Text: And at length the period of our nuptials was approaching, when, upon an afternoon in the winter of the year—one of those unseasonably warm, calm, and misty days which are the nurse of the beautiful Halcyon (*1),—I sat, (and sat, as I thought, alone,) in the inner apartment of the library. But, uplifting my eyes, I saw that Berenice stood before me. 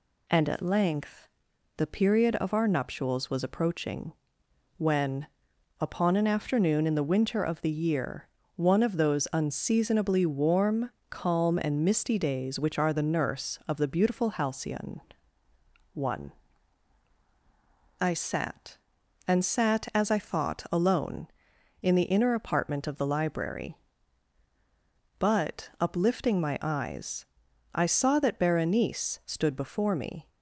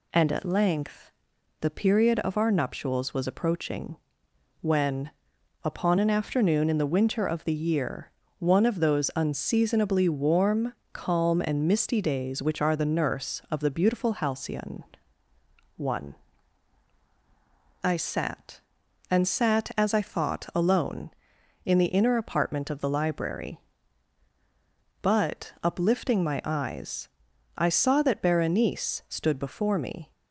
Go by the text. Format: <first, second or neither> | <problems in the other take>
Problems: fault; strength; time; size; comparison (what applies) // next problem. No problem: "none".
neither | pauses between "length" and "the"; noticeable; the same in both